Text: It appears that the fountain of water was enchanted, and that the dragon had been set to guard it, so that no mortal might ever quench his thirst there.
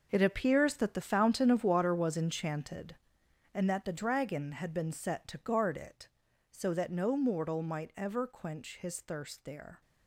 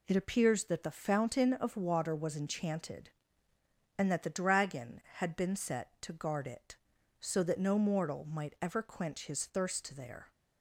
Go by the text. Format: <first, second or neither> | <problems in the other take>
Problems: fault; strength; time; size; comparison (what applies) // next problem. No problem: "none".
second | gets quieter; strong; throughout; 12.5 dB